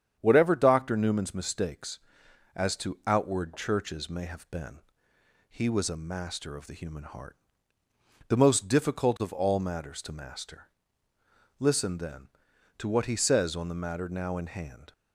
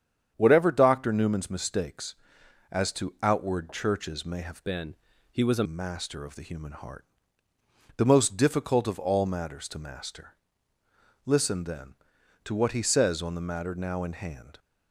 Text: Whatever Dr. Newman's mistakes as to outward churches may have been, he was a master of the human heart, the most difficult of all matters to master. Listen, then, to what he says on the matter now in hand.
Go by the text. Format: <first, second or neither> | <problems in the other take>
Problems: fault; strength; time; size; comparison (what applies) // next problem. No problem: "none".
first | starts louder than the rest; strong; until 1.3 s; 8.5 dB; strong in the first // changes voice from "been" to "a"; from 4.6 to 5.6 s; 1.0 s long